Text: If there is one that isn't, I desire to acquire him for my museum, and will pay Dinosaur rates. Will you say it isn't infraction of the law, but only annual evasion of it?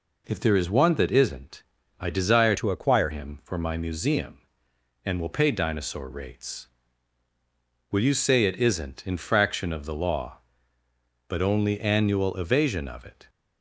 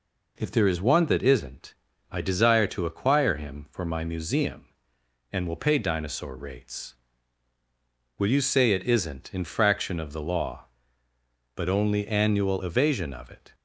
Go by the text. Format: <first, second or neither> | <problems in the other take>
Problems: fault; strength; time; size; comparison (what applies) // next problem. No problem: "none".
second | changes voice from "to" to "acquire"; from 2.5 to 3.0 s; 0.5 s long